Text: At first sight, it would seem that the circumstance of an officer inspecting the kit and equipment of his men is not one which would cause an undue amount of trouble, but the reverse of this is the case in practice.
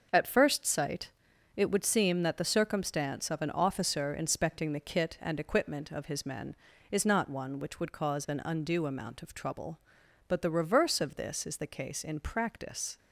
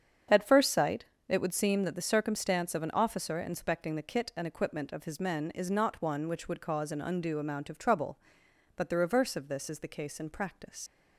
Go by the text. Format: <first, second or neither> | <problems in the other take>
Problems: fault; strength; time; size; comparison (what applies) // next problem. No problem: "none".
first | starts louder than the rest; strong; until 1.5 s; 7.5 dB; noticeable in the first // leaves "practice" unfinished; at 10.8 s; 105 ms